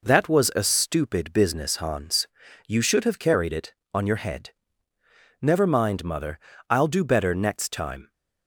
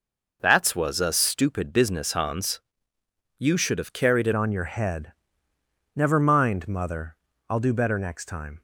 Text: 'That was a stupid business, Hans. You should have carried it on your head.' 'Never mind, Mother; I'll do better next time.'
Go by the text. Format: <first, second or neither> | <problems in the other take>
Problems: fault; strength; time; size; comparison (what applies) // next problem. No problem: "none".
first | changes voice at "on"; from 4.3 s on; 4.3 s long